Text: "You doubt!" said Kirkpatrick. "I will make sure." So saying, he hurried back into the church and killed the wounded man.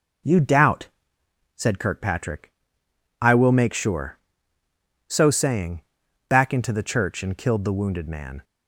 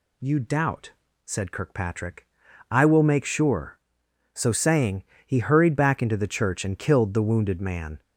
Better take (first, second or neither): second